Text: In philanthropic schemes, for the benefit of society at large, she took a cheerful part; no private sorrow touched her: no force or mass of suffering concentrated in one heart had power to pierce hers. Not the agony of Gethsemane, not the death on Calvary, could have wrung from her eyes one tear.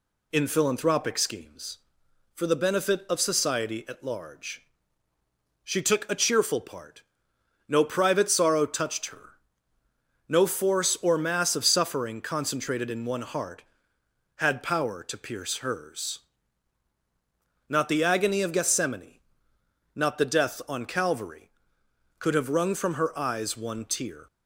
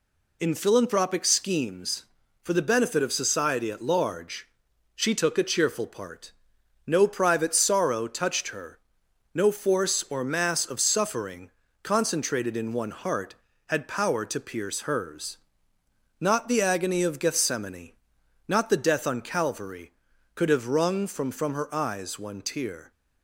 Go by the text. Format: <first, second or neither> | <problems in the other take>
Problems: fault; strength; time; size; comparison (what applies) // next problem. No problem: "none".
first | pauses between "suffering" and "concentrated"; slight; at 11.5 s; 0.32 s long // says "from" twice; at 21.3 s